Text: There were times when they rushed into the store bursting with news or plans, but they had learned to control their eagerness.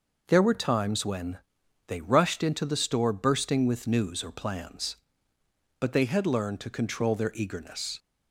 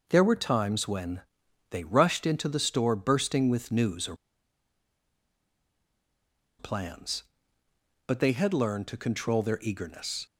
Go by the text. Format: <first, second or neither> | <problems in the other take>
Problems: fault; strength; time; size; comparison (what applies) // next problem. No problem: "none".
first | pauses between "when" and "they"; noticeable; at 1.2 s; 0.48 s long; noticeable in the first // pauses between "or" and "plans"; strong; at 4.1 s; 2.4 s long